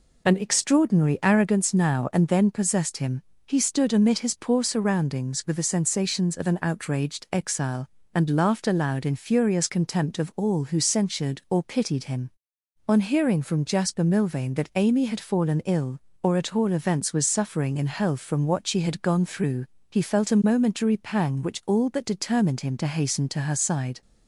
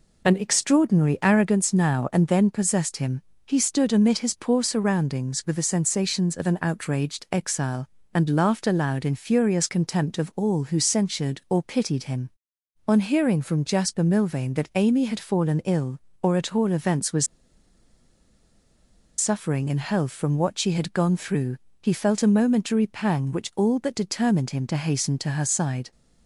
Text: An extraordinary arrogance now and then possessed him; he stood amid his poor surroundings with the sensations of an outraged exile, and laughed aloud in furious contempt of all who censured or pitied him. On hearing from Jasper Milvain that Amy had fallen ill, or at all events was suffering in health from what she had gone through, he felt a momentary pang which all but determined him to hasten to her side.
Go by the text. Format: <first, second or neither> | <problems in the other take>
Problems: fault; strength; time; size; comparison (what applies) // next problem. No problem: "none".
first | pauses between "was" and "suffering"; strong; at 17.2 s; 1.9 s long